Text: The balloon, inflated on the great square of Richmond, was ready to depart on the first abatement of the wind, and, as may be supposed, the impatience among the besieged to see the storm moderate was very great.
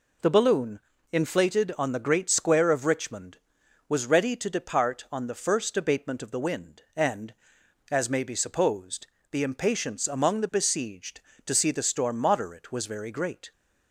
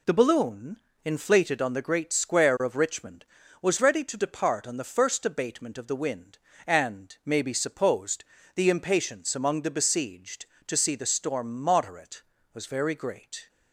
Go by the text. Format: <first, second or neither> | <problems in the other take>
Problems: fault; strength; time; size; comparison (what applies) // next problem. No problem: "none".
first | skips "as"; at 7.2 s